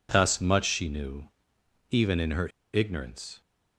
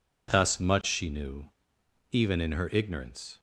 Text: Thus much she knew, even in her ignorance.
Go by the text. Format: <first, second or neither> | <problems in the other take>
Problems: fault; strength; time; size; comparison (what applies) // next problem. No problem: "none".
second | pauses between "her" and "ignorance"; slight; at 2.4 s; 0.25 s long